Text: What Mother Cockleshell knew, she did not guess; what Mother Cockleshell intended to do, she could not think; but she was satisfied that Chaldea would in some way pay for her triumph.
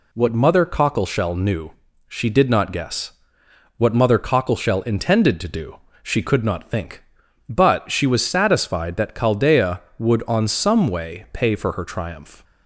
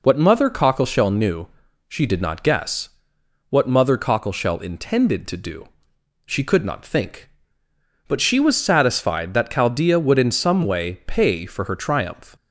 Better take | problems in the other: second | says "on" for "in"; at 10.2 s

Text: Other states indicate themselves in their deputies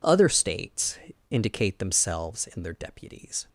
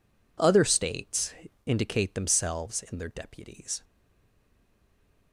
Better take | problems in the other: first | pauses between "states" and "indicate"; slight; at 1.3 s; 0.32 s long; slight in the first // stays silent after the last word; noticeable; from 3.8 s on; 1.5 s long

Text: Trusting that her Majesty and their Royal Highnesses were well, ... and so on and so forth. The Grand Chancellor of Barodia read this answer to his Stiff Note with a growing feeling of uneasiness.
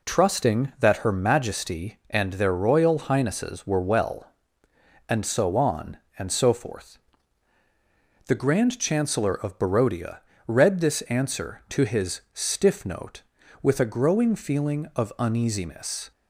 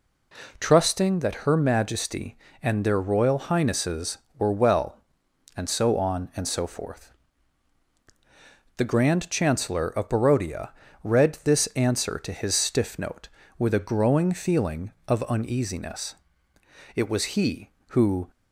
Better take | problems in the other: first | pauses between "Barodia" and "read"; slight; at 10.7 s; 0.32 s long; slight in the first // goes on to say "It was he who"; from 16.9 s on; 1.3 s long

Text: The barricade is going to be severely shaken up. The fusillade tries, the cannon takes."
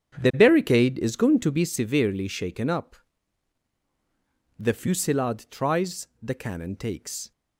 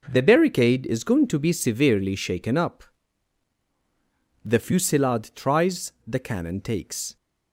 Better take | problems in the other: second | starts louder than the rest; strong; until 1.7 s; 8 dB

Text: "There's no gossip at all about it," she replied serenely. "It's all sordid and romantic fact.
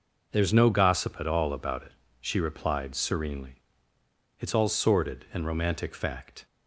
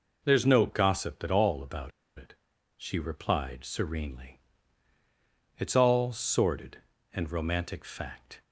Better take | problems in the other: first | pauses between "about" and "it"; slight; at 1.9 s; 0.27 s long

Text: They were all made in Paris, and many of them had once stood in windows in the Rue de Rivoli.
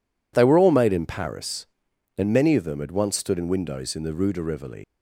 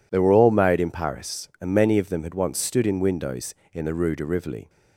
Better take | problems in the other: second | leaves "Rivoli" unfinished; at 4.8 s; 100 ms

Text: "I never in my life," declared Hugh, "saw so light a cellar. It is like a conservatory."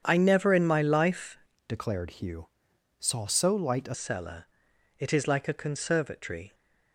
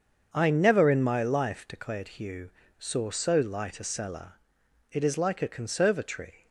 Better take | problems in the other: second | starts louder than the rest; strong; until 1.0 s; 8 dB; also in the second // changes voice from "declared" to "a"; from 1.6 to 3.9 s; 2.3 s long

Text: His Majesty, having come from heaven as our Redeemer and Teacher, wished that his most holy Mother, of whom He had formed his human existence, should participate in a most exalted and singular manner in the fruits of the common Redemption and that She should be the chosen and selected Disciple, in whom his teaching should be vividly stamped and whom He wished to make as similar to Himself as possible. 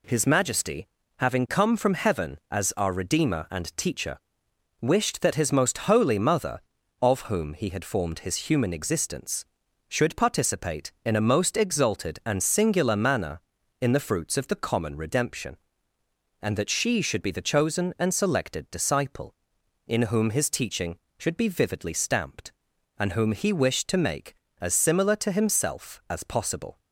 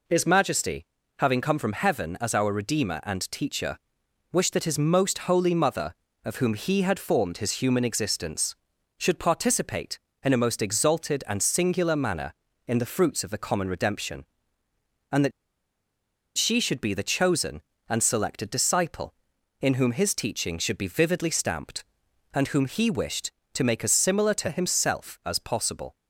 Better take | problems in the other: first | pauses between "that" and "She"; at 15.3 s; 1.0 s long

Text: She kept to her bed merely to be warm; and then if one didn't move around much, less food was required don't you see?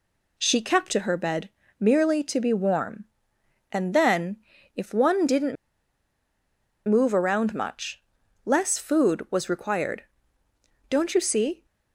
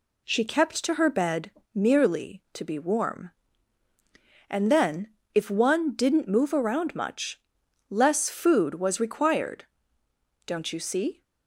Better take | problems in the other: second | pauses between "bed" and "merely"; slight; at 1.4 s; 0.30 s long; slight in the second // pauses between "then" and "if"; at 4.3 s; 0.38 s long; slight in the second // pauses between "didn't" and "move"; strong; at 5.5 s; 1.3 s long // pauses between "required" and "don't"; noticeable; at 10.0 s; 0.84 s long; noticeable in the second

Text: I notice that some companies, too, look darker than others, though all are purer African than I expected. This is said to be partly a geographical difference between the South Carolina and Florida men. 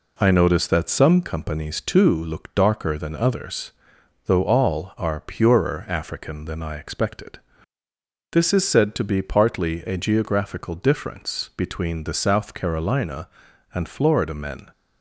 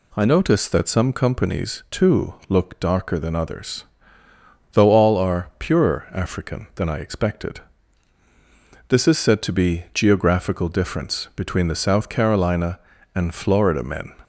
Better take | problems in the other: first | skips "partly a"; at 9.8 s

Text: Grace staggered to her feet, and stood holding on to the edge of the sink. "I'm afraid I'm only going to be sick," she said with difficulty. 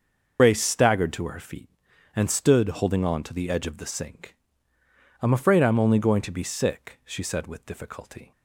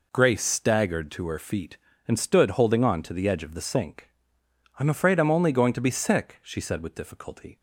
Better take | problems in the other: second | loses the start of "Grace"; at 0.3 s; 85 ms // starts louder than the rest; until 1.4 s; 6 dB

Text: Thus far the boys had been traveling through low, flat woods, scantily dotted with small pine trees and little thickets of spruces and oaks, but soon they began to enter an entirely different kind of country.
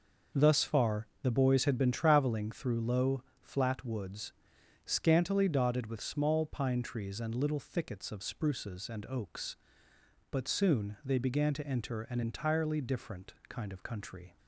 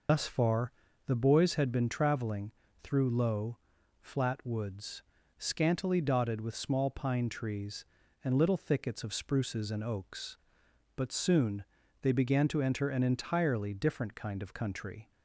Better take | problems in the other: first | loses the start of "Thus"; at 0.0 s; 100 ms // pauses between "far" and "the"; slight; at 0.7 s; 0.36 s long; slight in the first // pauses between "traveling" and "through"; slight; at 2.5 s; 0.30 s long // pauses between "soon" and "they"; at 11.6 s; 0.38 s long

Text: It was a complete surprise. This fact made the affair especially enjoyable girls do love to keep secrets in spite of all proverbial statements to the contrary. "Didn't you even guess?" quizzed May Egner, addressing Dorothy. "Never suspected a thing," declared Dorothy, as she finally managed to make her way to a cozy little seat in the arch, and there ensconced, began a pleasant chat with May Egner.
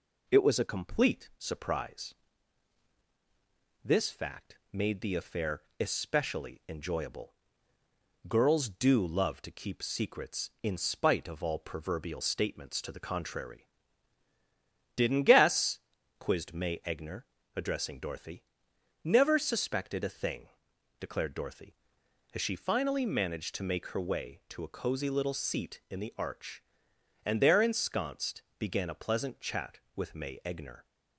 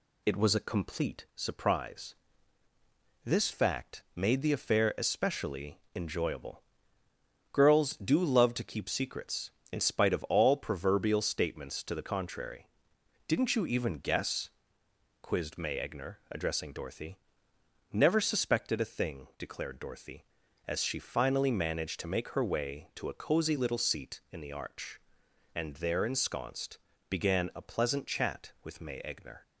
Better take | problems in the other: second | pauses between "fact" and "made"; slight; at 4.5 s; 0.16 s long // pauses between "affair" and "especially"; slight; at 5.6 s; 0.18 s long // pauses between "enjoyable" and "girls"; noticeable; at 7.3 s; 0.94 s long; noticeable in the second // skips "you even"; at 15.2 s

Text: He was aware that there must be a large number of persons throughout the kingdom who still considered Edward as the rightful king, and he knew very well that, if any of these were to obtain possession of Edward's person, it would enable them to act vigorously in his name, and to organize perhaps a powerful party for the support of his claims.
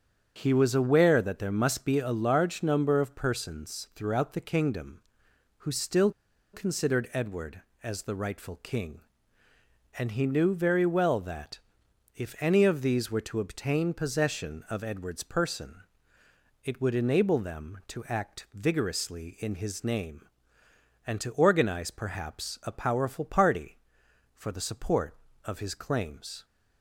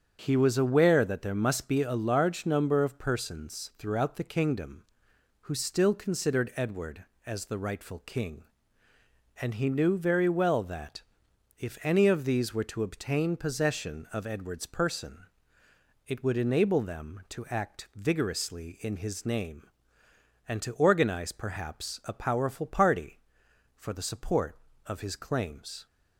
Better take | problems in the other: second | starts louder than the rest; until 1.3 s; 7 dB; also in the second // pauses between "still" and "considered"; at 6.1 s; 0.42 s long

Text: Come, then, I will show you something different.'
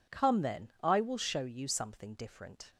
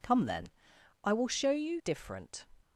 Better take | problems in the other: first | skips "something"; at 1.8 s

